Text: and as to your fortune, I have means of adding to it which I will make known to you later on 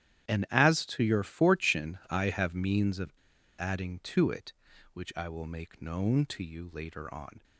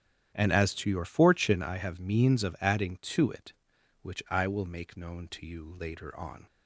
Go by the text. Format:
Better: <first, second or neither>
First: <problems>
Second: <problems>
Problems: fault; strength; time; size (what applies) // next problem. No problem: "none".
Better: second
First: starts louder than the rest; strong; until 1.3 s; 11 dB // pauses between "of" and "adding"; noticeable; at 3.1 s; 0.46 s long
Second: starts louder than the rest; strong; until 1.3 s; 10 dB